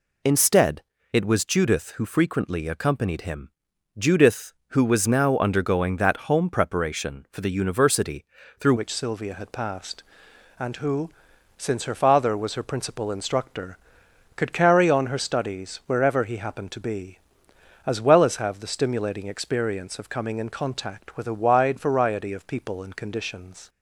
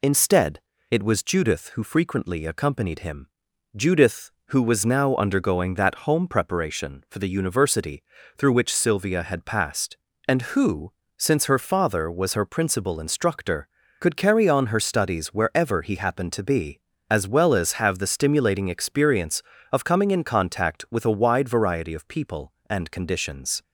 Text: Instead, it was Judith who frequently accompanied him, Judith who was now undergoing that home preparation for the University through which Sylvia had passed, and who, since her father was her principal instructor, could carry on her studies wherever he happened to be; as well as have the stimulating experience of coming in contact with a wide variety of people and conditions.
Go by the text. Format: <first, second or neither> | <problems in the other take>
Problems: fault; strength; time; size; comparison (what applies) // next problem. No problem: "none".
second | pauses between "University" and "through"; slight; at 8.2 s; 0.36 s long; slight in the second // changes voice at "which"; from 8.7 s on; 14.9 s long